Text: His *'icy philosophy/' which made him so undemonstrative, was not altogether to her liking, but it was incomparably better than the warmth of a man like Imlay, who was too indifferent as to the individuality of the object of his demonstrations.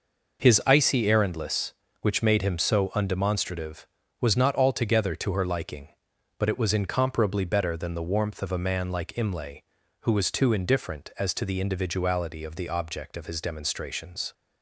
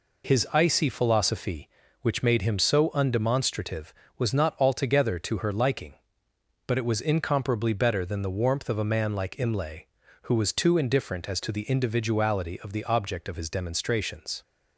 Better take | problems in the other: second | says "errandless" for "philosophy"; at 1.0 s

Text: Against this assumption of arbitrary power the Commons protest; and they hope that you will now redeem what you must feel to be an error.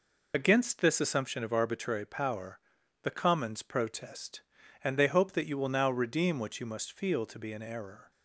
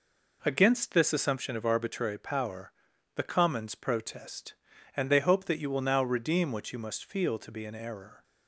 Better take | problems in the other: second | loses the start of "Against"; at 0.3 s; 55 ms // pauses between "power" and "the"; at 2.5 s; 0.44 s long; also in the second

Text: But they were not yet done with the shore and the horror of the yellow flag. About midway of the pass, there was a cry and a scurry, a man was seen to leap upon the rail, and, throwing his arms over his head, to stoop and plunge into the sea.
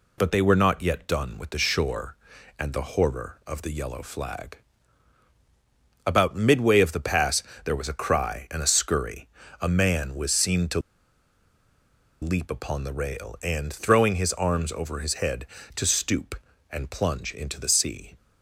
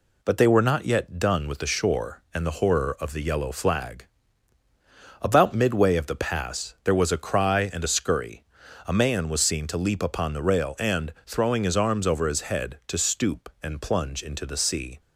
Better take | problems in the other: second | pauses between "to" and "leap"; strong; at 10.7 s; 1.4 s long

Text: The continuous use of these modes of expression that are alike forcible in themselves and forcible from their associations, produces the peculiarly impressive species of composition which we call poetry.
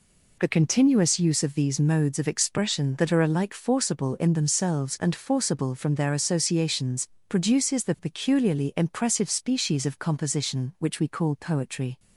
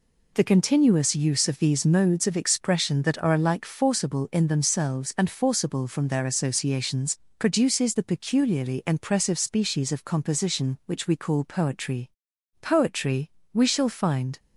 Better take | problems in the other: first | goes on to say "Poetry we shall find"; strong; from 12.6 s on; 1.7 s long

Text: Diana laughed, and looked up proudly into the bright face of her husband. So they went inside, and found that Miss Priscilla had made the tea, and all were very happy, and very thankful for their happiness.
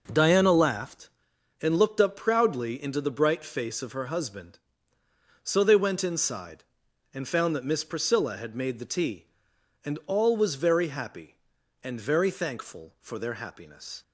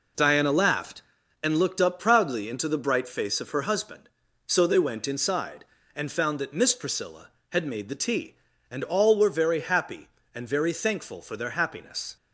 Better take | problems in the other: second | says "was" for "were"; at 10.3 s

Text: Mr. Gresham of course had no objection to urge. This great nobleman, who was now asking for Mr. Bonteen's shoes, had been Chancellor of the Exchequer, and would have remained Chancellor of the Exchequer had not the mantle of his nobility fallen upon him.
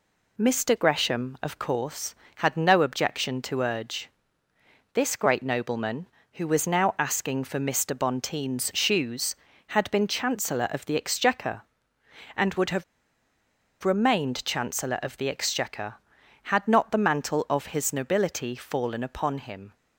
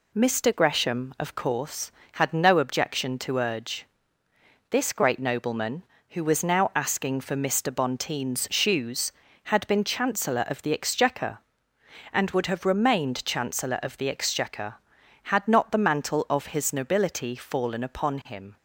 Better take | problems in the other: second | pauses between "have" and "remained"; at 12.8 s; 0.99 s long

